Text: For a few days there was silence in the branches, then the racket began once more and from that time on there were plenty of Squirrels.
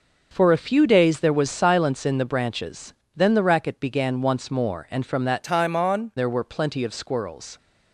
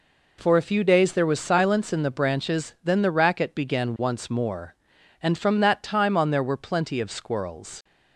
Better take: second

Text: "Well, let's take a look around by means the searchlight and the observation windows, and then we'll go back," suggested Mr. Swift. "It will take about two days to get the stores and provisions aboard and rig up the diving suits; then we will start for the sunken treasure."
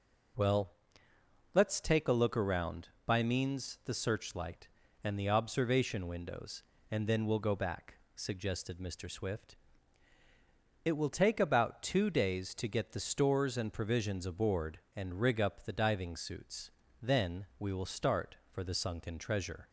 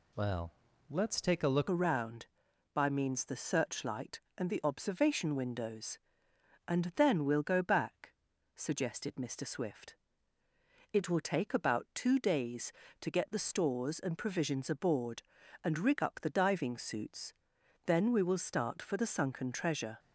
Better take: first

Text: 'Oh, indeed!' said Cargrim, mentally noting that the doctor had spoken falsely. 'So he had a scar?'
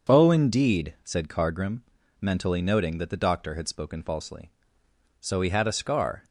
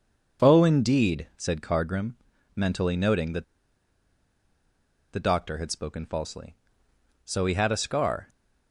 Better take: first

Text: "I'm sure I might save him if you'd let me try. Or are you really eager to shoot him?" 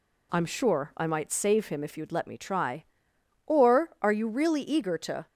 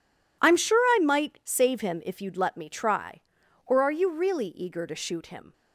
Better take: second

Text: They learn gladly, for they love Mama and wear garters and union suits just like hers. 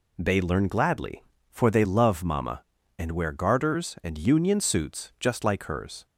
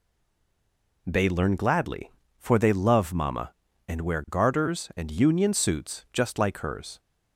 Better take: first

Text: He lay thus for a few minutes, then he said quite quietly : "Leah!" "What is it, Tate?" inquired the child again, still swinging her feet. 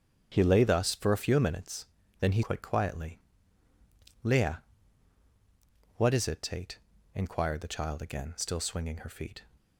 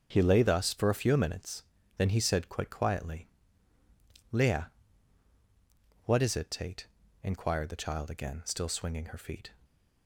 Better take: second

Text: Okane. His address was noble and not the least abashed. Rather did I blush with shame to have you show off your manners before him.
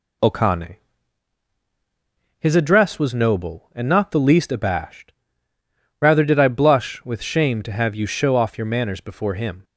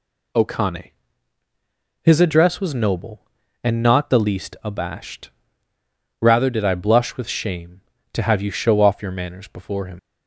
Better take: first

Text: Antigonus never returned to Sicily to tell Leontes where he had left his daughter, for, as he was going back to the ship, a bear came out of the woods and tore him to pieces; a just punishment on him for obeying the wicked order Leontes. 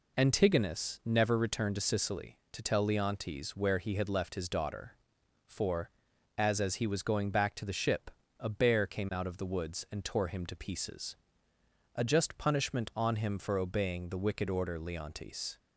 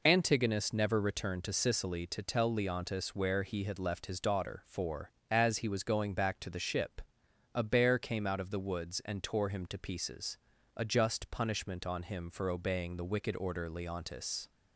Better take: second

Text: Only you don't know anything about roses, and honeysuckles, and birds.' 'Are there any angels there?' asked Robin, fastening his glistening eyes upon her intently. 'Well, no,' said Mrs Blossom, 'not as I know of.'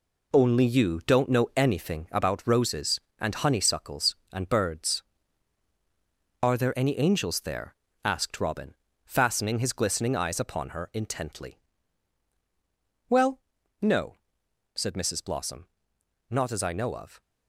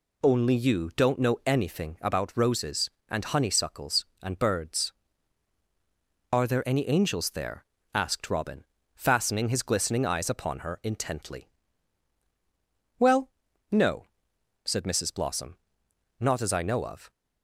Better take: second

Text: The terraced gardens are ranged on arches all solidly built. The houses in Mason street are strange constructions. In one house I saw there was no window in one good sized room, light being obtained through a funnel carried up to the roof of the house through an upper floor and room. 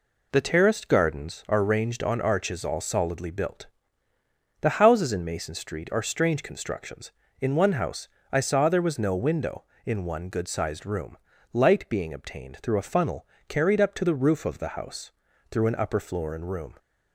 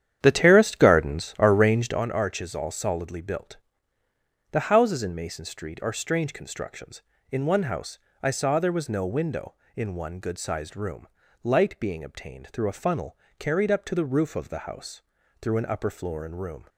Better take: first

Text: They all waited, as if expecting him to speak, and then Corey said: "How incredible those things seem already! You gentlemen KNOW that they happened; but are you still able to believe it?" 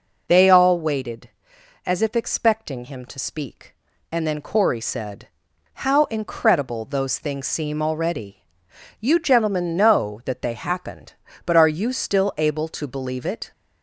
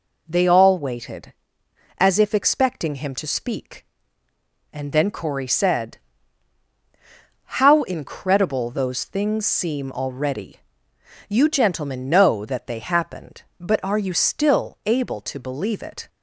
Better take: neither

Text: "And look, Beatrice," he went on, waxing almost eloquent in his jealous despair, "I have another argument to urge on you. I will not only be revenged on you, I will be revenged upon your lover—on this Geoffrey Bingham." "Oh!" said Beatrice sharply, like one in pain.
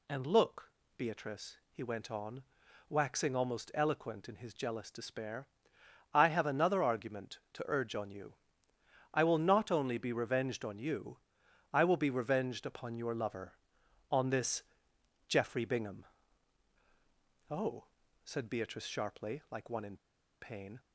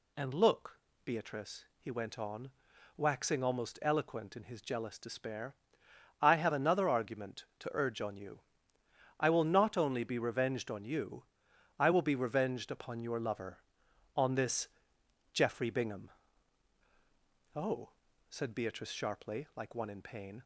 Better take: second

